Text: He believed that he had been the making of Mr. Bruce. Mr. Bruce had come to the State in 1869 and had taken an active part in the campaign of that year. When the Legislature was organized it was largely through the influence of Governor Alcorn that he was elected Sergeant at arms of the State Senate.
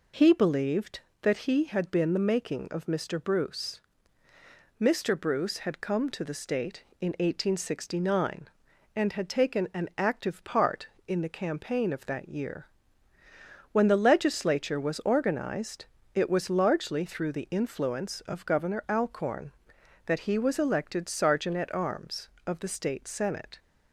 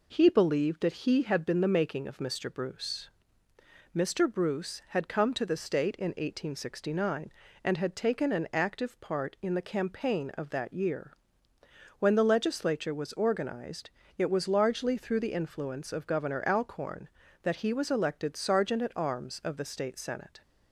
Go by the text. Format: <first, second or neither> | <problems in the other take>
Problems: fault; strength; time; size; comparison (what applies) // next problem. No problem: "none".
neither | pauses between "organized" and "it"; slight; the same in both